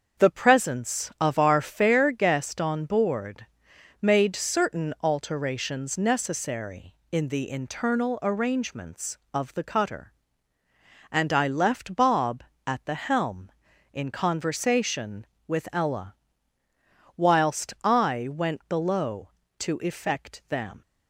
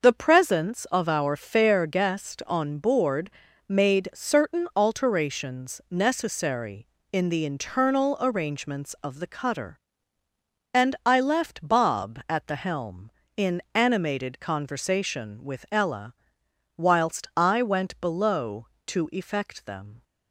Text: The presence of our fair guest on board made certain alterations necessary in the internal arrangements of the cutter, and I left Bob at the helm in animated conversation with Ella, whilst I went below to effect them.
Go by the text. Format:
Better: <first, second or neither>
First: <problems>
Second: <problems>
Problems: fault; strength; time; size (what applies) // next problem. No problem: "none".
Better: second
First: starts louder than the rest; until 1.2 s; 7 dB // pauses between "board" and "made"; noticeable; at 3.4 s; 0.56 s long // skips "animated"; at 14.0 s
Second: pauses between "board" and "made"; slight; at 3.3 s; 0.36 s long